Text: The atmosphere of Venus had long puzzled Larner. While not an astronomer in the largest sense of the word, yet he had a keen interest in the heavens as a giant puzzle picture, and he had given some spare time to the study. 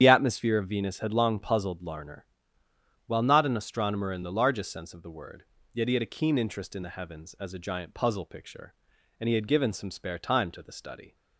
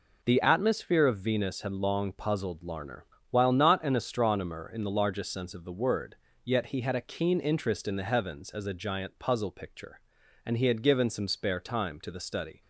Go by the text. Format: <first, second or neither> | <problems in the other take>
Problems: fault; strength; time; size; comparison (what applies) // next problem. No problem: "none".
second | loses the start of "The"; at 0.0 s; 55 ms // starts louder than the rest; strong; until 1.0 s; 9 dB